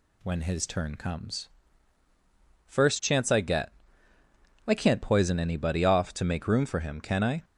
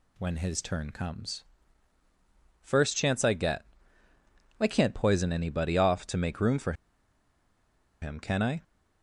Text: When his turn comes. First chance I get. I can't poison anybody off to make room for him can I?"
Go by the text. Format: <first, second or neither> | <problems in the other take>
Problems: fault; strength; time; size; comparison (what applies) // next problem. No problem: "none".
first | pauses between "for" and "him"; strong; at 6.7 s; 1.2 s long